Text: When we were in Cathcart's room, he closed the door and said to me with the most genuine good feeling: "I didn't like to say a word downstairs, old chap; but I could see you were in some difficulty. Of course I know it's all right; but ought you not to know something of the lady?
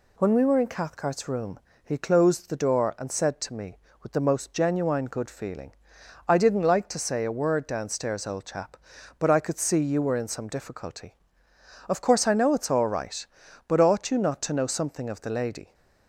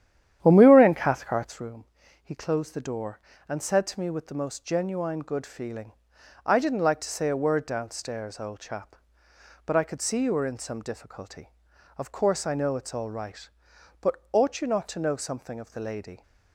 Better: first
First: none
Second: starts louder than the rest; strong; until 1.7 s; 10.5 dB // pauses between "but" and "ought"; slight; at 14.1 s; 0.16 s long

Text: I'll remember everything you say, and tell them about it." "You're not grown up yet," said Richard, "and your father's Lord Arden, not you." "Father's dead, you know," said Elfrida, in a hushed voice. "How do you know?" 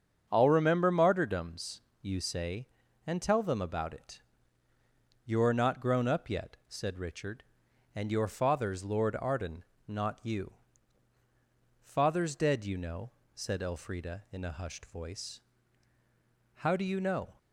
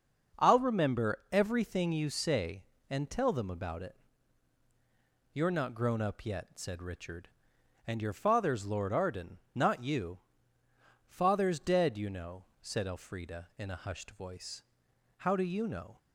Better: second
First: starts louder than the rest; until 1.3 s; 7 dB // says "martyrdoms" for "everything"; at 0.9 s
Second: starts louder than the rest; noticeable; until 1.5 s; 6 dB

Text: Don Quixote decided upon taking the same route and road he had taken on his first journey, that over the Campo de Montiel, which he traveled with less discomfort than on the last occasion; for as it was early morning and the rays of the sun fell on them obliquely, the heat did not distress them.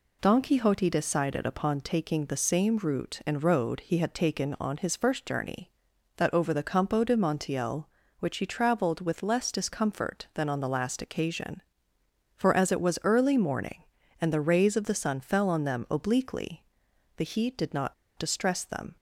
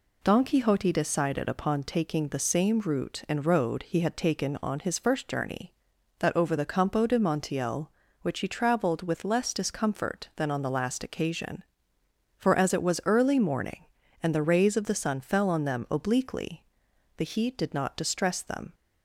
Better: second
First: pauses between "not" and "distress"; slight; at 17.9 s; 0.23 s long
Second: none

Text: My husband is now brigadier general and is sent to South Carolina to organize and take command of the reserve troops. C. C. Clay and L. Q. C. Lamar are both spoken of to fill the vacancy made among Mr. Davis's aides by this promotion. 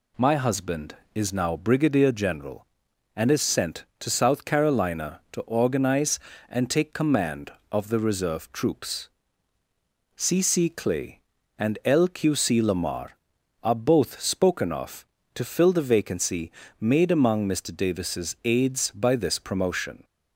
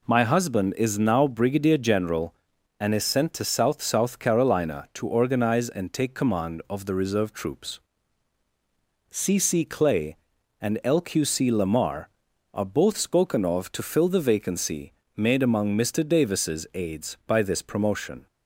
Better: first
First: pauses between "vacancy" and "made"; slight; at 16.5 s; 0.26 s long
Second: says "South" twice; at 3.8 s // pauses between "vacancy" and "made"; slight; at 14.9 s; 0.24 s long

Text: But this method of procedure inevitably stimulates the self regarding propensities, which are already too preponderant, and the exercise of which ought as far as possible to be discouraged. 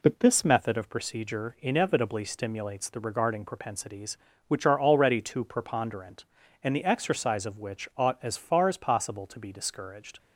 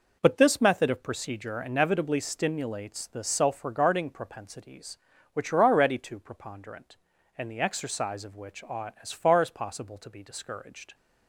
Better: second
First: skips "self"; at 3.0 s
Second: none

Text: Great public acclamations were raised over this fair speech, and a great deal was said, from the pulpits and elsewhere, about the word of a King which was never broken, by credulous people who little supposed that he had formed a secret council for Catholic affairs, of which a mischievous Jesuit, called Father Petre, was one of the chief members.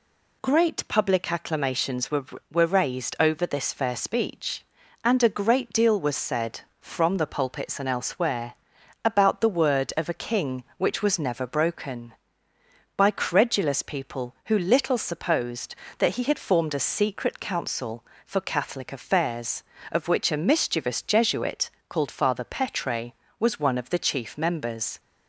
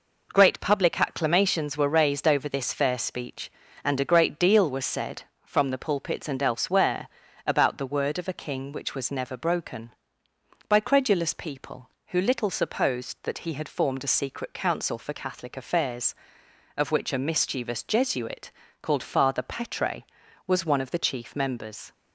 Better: second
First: says "were" twice; at 2.4 s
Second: none

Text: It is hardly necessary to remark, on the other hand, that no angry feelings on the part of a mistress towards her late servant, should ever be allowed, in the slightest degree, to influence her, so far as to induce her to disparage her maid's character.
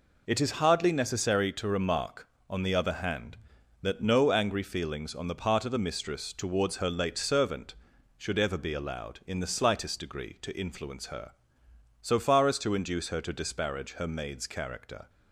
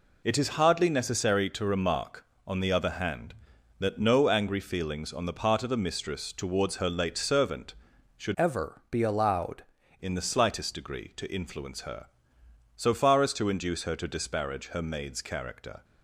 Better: first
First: none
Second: changes voice from "ever" to "allowed"; from 8.3 to 9.6 s; 1.3 s long

